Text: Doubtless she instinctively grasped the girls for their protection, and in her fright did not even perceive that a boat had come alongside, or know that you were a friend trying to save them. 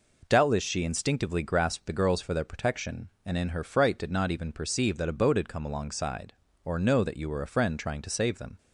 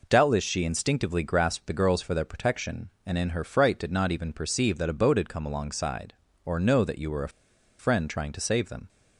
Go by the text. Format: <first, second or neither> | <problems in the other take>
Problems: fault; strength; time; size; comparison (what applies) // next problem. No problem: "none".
first | pauses between "a" and "friend"; noticeable; at 7.2 s; 0.50 s long